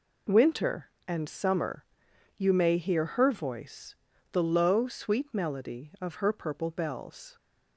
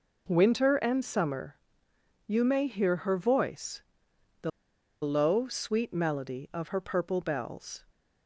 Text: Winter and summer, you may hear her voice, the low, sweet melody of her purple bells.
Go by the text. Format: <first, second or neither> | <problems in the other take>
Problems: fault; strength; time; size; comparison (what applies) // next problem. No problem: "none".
first | pauses between "the" and "low"; noticeable; at 4.4 s; 0.52 s long